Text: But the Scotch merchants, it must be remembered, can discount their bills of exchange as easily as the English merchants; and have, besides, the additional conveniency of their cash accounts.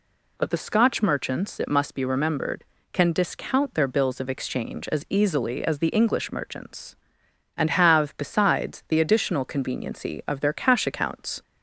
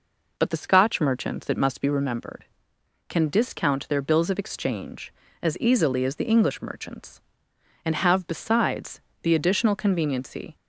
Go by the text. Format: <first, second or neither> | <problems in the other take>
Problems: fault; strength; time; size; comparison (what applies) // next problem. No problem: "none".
first | stops before "of their cash accounts"; at 10.5 s